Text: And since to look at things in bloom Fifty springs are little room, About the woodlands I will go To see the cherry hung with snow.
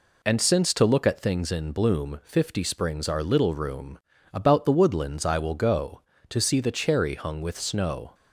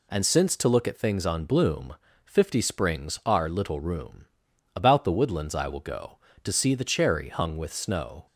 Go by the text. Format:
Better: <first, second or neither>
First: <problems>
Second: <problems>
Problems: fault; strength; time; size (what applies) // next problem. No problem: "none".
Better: first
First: none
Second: says "on" for "in"; at 1.2 s // pauses between "bloom" and "Fifty"; slight; at 1.9 s; 0.30 s long